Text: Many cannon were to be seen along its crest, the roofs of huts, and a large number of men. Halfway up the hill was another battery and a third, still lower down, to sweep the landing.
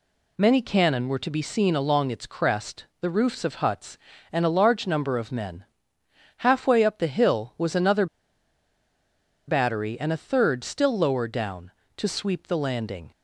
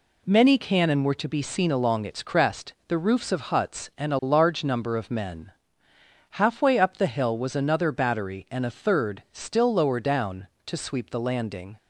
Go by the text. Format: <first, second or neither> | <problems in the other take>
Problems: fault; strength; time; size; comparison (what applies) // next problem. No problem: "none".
second | pauses between "another" and "battery"; strong; at 8.0 s; 1.4 s long